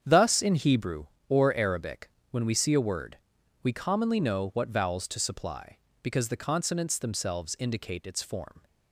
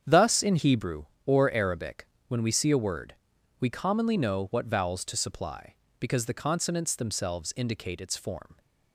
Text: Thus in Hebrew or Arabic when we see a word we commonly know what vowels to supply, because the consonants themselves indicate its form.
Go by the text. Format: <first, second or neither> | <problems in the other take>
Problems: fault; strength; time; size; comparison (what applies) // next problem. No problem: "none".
neither | starts louder than the rest; strong; the same in both // pauses between "Arabic" and "when"; slight; the same in both // pauses between "word" and "we"; the same in both